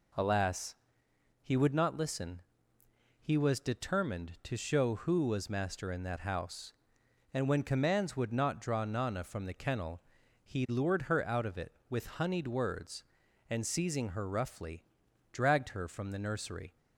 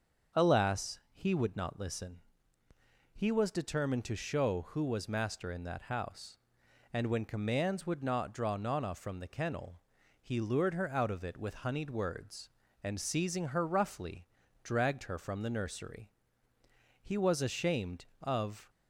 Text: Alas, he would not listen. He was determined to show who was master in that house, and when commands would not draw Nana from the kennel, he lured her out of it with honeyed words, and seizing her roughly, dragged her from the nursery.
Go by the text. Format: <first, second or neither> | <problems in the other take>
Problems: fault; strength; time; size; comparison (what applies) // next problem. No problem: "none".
first | starts louder than the rest; until 1.4 s; 6.5 dB // goes on to say "He was ashamed of"; from 17.0 s on; 1.6 s long